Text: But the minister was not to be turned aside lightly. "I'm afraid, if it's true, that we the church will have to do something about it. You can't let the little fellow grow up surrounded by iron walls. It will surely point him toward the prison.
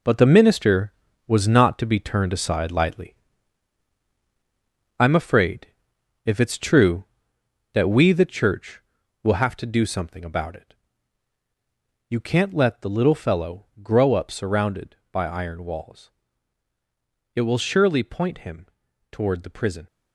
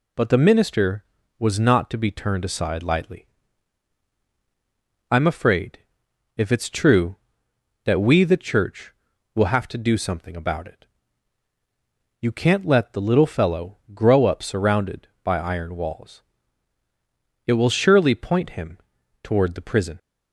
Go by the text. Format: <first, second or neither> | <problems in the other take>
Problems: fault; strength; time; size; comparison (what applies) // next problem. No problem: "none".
second | gets quieter; strong; throughout; 9 dB // pauses between "him" and "toward"; noticeable; at 18.6 s; 0.46 s long; noticeable in the second